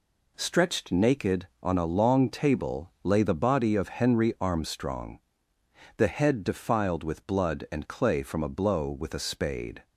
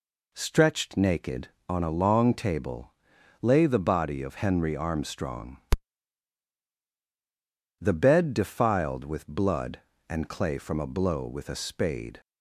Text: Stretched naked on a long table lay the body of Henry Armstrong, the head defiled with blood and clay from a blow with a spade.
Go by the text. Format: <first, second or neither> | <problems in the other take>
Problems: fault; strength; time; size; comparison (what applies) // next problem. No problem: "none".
first | pauses between "table" and "lay"; noticeable; at 2.9 s; 0.50 s long // says "bed" for "head"; at 7.9 s